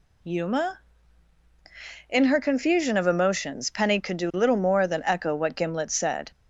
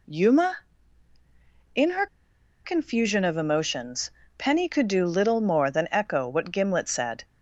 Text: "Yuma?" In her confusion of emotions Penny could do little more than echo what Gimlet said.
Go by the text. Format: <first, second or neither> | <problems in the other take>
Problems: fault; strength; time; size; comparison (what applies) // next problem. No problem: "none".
first | pauses between "her" and "confusion"; noticeable; at 2.0 s; 0.57 s long // pauses between "emotions" and "Penny"; slight; at 4.1 s; 0.28 s long